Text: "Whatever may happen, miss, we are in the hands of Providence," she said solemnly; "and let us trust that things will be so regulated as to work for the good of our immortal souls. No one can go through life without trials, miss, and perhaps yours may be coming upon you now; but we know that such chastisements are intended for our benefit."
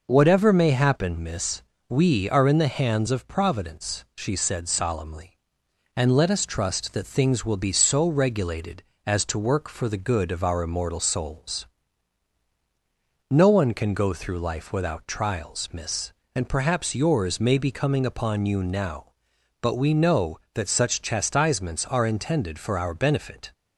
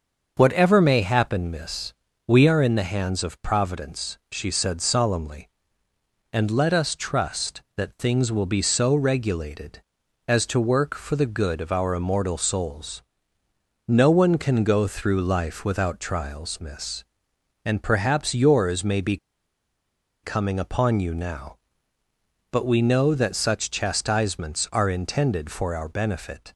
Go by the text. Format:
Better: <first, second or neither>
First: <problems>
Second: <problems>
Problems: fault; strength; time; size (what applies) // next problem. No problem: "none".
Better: first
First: none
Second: starts louder than the rest; until 1.3 s; 6.5 dB // pauses between "be" and "coming"; at 19.1 s; 1.0 s long